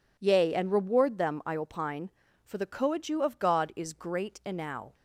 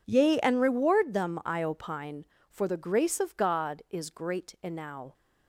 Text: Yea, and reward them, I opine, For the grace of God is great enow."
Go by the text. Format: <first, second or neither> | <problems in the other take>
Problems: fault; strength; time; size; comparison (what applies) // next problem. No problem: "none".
second | says "coadju" for "grace"; at 2.6 s